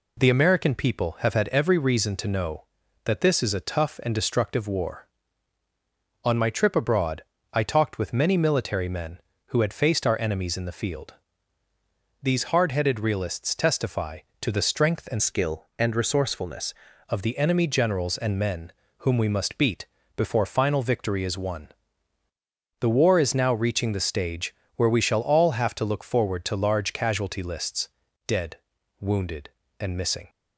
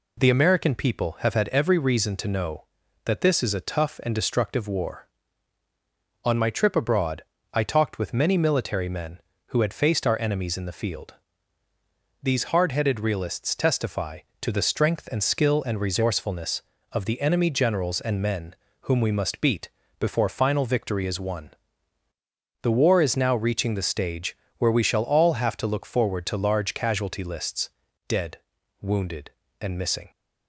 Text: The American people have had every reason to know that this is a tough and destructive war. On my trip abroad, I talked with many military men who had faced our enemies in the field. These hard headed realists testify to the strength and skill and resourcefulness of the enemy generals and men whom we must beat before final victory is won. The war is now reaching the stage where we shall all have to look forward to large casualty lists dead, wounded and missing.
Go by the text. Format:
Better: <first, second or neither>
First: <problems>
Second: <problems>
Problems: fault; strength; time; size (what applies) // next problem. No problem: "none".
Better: second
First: changes voice from "skill" to "resourcefulness"; from 15.1 to 16.7 s; 1.6 s long // pauses between "men" and "whom"; slight; at 18.7 s; 0.26 s long // pauses between "beat" and "before"; slight; at 19.8 s; 0.32 s long // pauses between "stage" and "where"; slight; at 24.5 s; 0.22 s long // pauses between "lists" and "dead"; at 27.8 s; 0.40 s long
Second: pauses between "men" and "whom"; slight; at 18.5 s; 0.26 s long // pauses between "beat" and "before"; slight; at 19.6 s; 0.32 s long // pauses between "stage" and "where"; slight; at 24.3 s; 0.22 s long // pauses between "lists" and "dead"; at 27.6 s; 0.40 s long